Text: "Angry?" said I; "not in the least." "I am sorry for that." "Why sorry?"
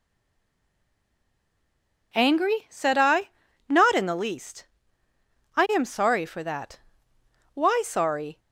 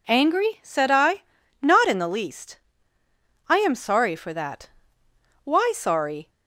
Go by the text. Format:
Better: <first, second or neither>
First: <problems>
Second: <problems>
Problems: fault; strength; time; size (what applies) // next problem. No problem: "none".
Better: second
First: stays silent before the first word; until 2.1 s; 2.1 s long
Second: none